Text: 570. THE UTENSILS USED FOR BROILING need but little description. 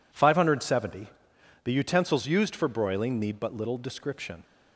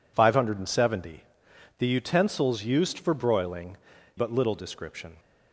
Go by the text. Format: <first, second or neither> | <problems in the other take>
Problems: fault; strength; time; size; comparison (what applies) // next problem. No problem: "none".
first | skips "need"; at 3.9 s